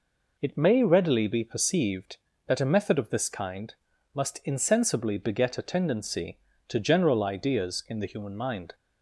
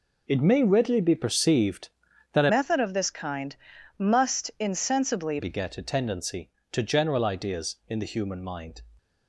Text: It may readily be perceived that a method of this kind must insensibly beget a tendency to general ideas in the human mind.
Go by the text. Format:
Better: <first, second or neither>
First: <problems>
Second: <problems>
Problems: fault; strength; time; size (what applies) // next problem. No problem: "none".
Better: first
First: pauses between "kind" and "must"; at 3.7 s; 0.40 s long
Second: changes voice from "method" to "insensibly"; from 2.5 to 5.3 s; 2.8 s long // pauses between "kind" and "must"; at 3.5 s; 0.42 s long